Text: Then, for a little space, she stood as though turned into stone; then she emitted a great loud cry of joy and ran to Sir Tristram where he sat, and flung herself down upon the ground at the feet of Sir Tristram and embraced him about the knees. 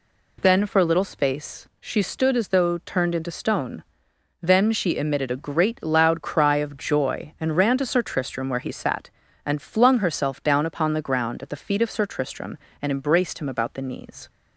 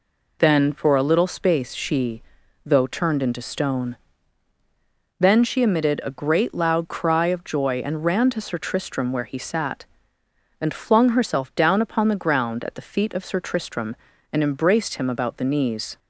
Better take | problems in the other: first | skips "stood as"; at 2.4 s

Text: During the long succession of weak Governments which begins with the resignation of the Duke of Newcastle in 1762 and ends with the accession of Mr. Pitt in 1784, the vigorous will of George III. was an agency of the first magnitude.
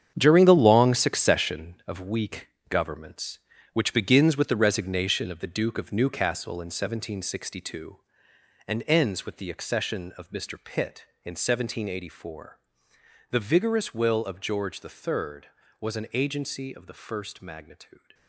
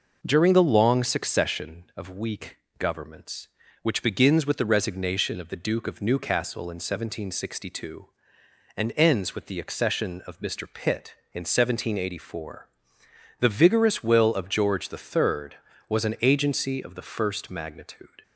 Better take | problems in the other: second | gets quieter; strong; throughout; 11 dB // pauses between "weak" and "Governments"; slight; at 2.4 s; 0.20 s long; slight in the second

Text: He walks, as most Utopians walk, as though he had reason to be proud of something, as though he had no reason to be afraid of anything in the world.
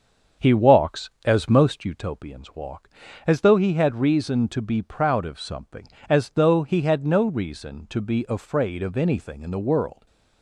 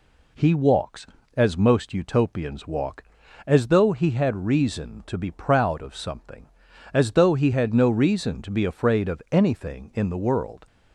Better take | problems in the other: second | starts louder than the rest; until 2.0 s; 7 dB

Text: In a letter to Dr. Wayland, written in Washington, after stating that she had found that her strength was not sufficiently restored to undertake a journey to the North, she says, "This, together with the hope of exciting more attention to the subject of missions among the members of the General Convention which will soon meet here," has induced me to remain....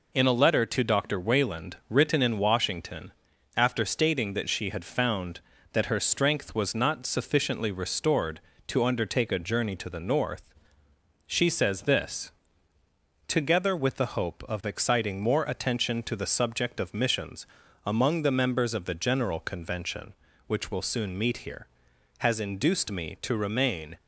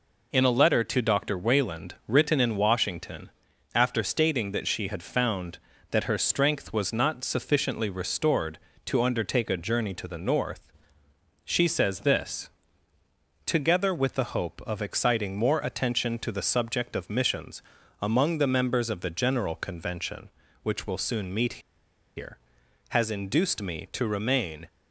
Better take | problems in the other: first | pauses between "missions" and "among"; at 17.6 s; 0.40 s long; also in the first // pauses between "meet" and "here"; noticeable; at 21.6 s; 0.57 s long

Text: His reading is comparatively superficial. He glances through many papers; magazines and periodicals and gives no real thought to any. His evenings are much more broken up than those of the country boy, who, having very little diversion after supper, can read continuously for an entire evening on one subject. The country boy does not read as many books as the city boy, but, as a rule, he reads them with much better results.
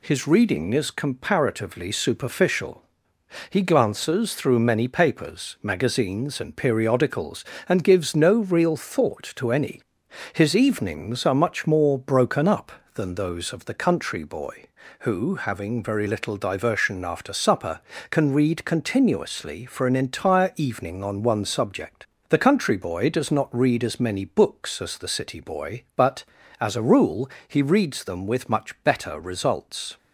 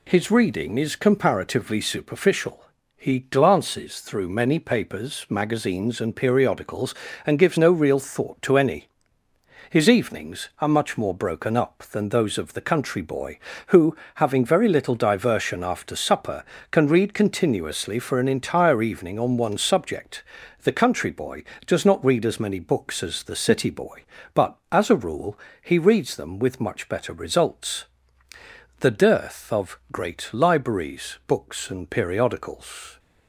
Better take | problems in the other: first | goes on to say "The dearth of great libraries books and periodicals"; strong; from 28.8 s on; 4.1 s long

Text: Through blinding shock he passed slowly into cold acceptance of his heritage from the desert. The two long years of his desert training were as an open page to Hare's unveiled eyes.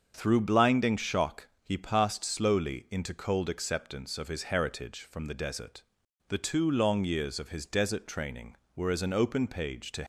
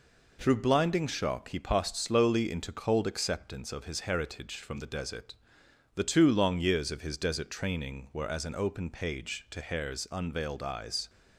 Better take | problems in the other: second | starts louder than the rest; until 1.1 s; 6.5 dB // stops before "Hare's unveiled eyes"; at 10.0 s

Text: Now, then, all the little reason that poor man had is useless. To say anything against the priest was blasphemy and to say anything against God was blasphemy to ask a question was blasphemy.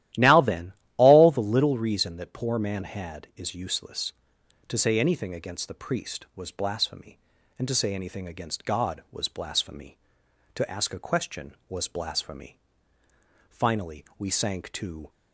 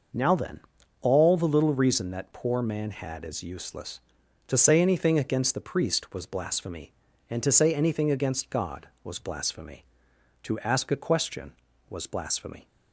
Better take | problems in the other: second | starts louder than the rest; strong; until 1.4 s; 13.5 dB // goes on to say "Finally we sank to"; from 13.4 s on; 1.6 s long

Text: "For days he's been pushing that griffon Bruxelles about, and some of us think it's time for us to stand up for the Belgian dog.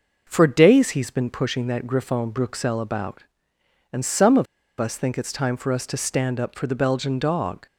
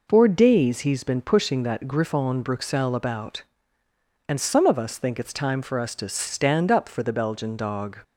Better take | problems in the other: second | pauses between "of" and "us"; slight; at 4.4 s; 0.34 s long

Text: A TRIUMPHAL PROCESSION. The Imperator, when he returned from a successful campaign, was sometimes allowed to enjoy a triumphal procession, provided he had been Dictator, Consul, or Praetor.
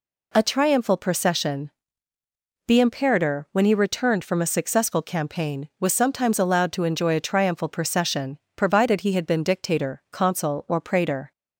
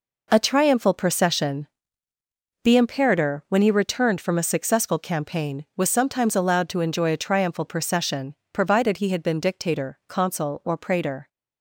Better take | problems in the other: first | gets quieter; strong; throughout; 7.5 dB

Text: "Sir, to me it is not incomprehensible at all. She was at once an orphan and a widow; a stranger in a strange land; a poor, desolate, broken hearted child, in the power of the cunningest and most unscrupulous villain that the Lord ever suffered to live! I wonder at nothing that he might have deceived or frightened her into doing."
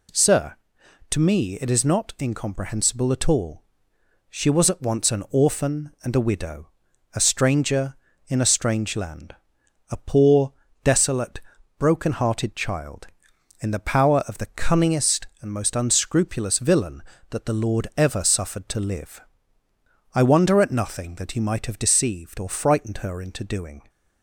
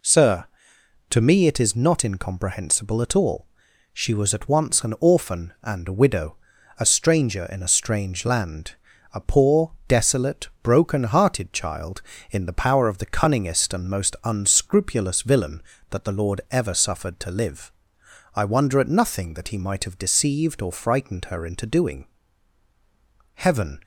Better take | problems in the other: first | goes on to say "Heaven"; slight; from 23.3 s on; 0.46 s long

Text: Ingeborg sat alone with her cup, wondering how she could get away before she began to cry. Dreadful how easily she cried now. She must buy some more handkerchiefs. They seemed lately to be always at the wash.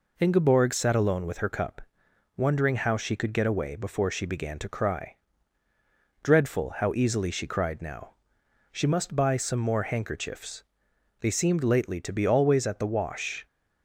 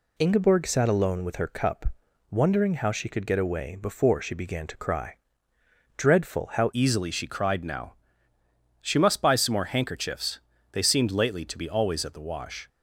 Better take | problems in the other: first | changes voice at "easily"; from 6.7 s on; 5.9 s long

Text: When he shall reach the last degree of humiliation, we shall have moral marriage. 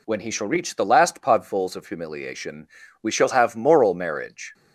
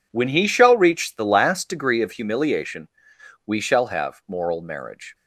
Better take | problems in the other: second | says "podfuls" for "degree"; at 1.1 s

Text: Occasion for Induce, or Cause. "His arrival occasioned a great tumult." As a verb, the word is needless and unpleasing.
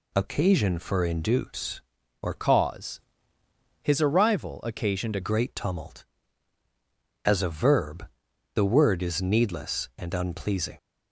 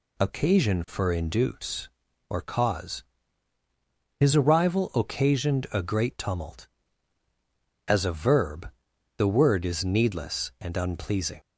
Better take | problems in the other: second | changes voice from "Cause" to "a"; from 2.3 to 5.1 s; 2.8 s long

